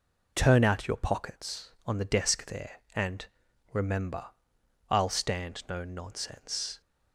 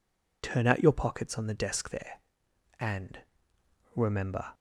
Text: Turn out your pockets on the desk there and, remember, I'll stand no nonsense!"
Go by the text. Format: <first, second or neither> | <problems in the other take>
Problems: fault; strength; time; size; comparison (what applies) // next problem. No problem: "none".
first | stops before "I'll stand no nonsense"; at 4.5 s